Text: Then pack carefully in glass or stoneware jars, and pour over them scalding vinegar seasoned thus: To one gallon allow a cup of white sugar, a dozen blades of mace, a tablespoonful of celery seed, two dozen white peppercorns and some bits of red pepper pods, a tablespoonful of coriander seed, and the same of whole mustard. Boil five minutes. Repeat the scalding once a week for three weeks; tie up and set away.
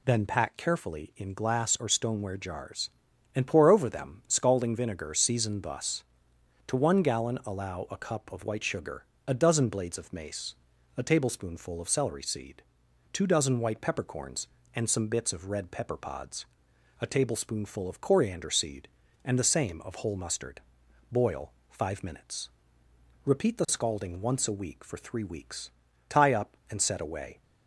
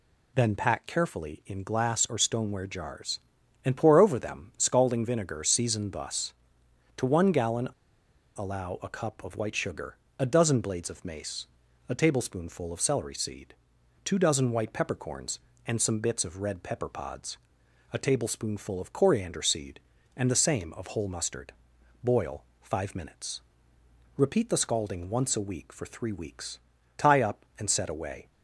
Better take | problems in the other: first | pauses between "gallon" and "allow"; noticeable; at 7.6 s; 0.68 s long // pauses between "Boil" and "five"; slight; at 22.4 s; 0.20 s long; slight in the first

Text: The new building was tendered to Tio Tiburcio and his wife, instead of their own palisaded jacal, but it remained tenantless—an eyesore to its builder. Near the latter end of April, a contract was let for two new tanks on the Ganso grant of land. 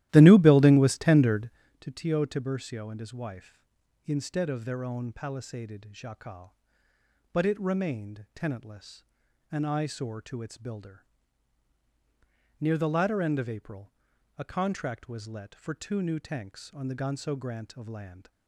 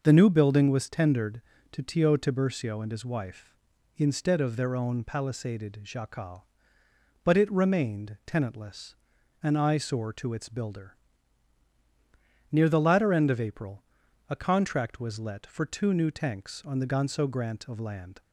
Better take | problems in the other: second | starts louder than the rest; strong; until 1.7 s; 14.5 dB

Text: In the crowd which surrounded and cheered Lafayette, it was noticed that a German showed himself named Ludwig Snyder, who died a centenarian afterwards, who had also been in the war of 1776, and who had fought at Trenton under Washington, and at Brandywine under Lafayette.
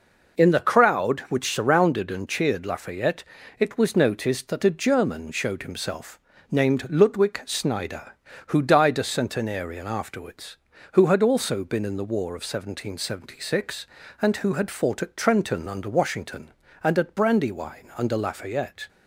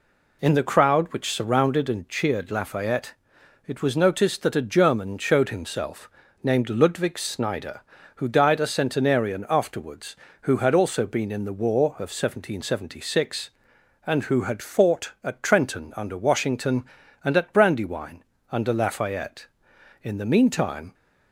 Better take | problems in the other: first | pauses between "himself" and "named"; slight; at 6.0 s; 0.32 s long; slight in the first // pauses between "Brandywine" and "under"; slight; at 18.2 s; 0.26 s long // goes on to say "In the meantime"; noticeable; from 20.0 s on; 0.92 s long

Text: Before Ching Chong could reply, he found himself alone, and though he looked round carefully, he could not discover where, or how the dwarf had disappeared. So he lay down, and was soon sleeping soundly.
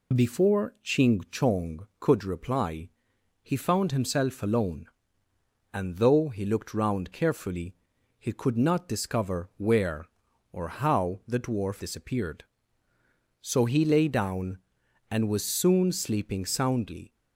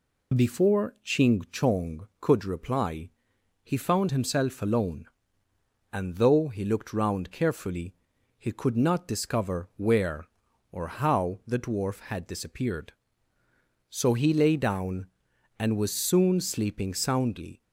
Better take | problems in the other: second | skips "had"; at 11.8 s

